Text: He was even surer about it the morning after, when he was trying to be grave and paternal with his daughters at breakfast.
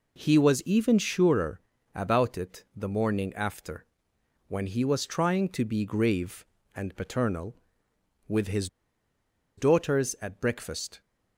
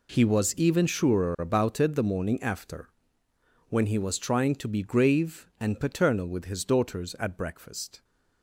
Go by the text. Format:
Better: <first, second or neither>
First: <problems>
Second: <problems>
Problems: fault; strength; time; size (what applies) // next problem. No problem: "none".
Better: second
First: pauses between "surer" and "about"; slight; at 1.6 s; 0.32 s long // pauses between "his" and "daughters"; noticeable; at 8.6 s; 0.90 s long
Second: none